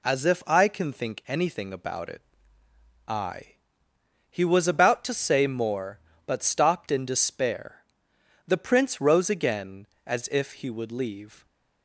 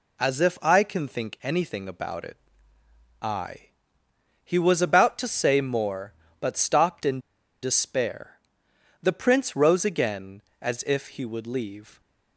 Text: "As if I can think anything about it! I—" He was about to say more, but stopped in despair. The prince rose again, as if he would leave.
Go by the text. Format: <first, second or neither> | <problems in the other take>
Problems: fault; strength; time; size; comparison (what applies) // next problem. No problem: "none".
first | pauses between "in" and "despair"; at 7.1 s; 0.43 s long